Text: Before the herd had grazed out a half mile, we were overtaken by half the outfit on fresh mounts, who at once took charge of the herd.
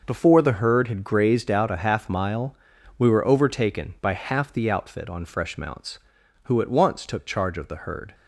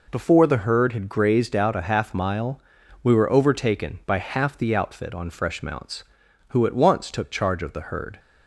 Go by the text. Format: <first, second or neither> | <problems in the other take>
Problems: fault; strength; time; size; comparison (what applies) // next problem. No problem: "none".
second | gets quieter; strong; throughout; 10.5 dB